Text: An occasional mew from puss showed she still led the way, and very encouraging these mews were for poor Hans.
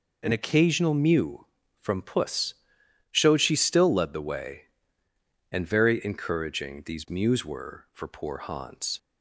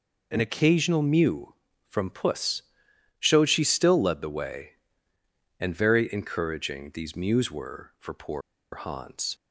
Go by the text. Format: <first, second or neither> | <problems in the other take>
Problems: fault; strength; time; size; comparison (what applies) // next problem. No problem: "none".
first | pauses between "puss" and "showed"; noticeable; at 2.6 s; 0.58 s long; noticeable in the first // pauses between "poor" and "Hans"; slight; at 8.4 s; 0.33 s long